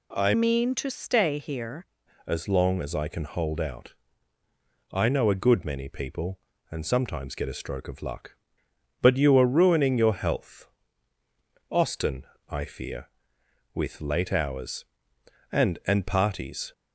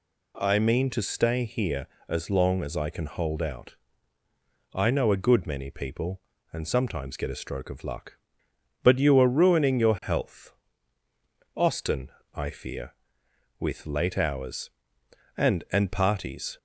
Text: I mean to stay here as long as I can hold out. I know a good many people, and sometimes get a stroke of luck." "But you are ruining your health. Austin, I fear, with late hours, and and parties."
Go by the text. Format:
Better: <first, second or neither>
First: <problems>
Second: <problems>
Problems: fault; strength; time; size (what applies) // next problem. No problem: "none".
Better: second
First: changes voice from "mean" to "here"; from 0.3 to 1.8 s; 1.5 s long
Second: none